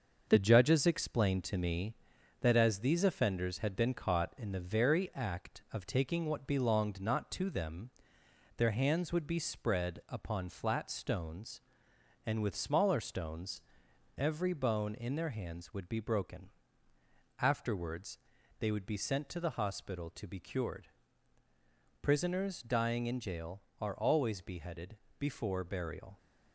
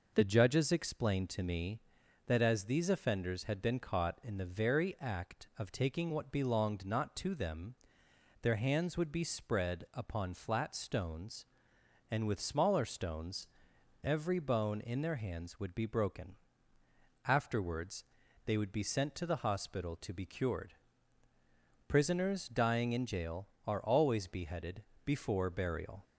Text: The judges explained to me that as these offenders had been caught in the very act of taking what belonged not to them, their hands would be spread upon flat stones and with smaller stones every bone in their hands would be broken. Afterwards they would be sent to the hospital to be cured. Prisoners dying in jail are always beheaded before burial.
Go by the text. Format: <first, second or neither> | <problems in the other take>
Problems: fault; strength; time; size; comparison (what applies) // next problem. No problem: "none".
second | gets quieter; noticeable; throughout; 5 dB // pauses between "stones" and "every"; noticeable; at 13.6 s; 0.56 s long; noticeable in the second // pauses between "Afterwards" and "they"; at 18.1 s; 0.42 s long; also in the second // pauses between "beheaded" and "before"; slight; at 24.9 s; 0.22 s long; slight in the second